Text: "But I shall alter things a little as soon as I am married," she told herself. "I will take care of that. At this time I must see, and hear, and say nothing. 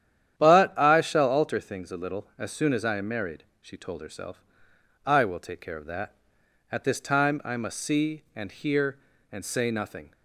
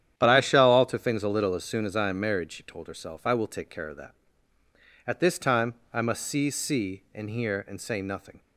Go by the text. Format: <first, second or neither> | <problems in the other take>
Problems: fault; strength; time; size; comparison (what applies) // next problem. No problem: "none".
first | starts louder than the rest; strong; until 1.1 s; 10 dB; strong in the first // pauses between "time" and "I"; slight; at 5.7 s; 0.18 s long // says "see" twice; at 6.4 s